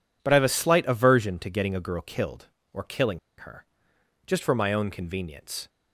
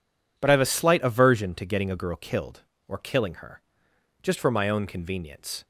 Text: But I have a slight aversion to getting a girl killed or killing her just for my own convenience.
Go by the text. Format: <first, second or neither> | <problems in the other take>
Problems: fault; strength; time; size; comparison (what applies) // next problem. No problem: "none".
second | pauses between "killing" and "her"; slight; at 3.1 s; 0.19 s long // pauses between "her" and "just"; noticeable; at 3.6 s; 0.62 s long; noticeable in the second